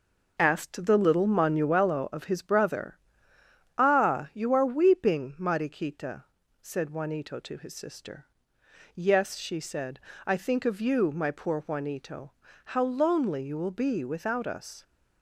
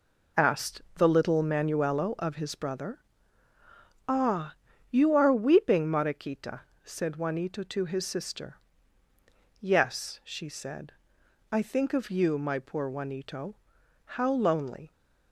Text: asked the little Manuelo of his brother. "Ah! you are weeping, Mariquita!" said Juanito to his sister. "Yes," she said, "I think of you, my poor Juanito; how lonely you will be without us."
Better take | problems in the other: first | stops before "you will be without us"; at 14.9 s

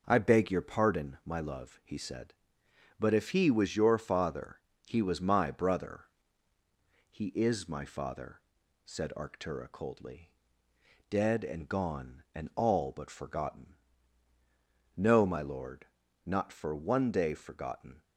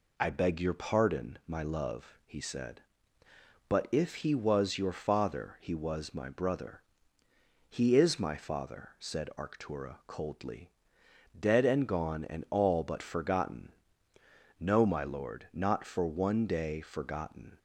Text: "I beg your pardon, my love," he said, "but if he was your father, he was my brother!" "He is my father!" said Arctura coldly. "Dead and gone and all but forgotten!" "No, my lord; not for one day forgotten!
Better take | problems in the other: neither | none

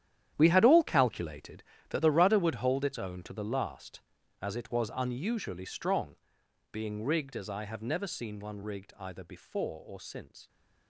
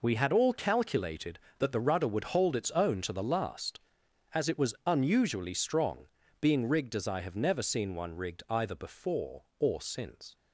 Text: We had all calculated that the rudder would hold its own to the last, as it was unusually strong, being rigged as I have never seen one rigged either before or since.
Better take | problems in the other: second | gets quieter; strong; throughout; 13 dB

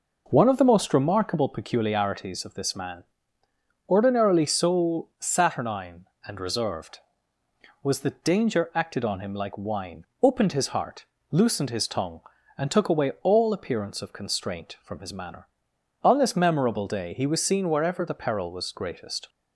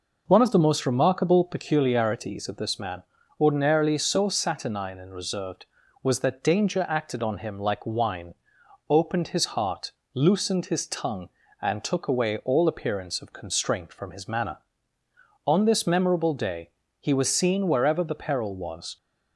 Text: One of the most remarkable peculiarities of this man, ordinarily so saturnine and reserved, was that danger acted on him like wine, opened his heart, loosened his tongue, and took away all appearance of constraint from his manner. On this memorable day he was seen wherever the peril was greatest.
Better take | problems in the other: first | pauses between "day" and "he"; slight; at 16.7 s; 0.28 s long // stops before "greatest"; at 18.9 s

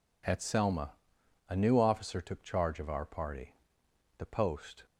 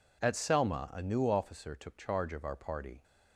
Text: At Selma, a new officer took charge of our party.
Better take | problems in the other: second | goes on to say "The post"; noticeable; from 4.1 s on; 0.68 s long

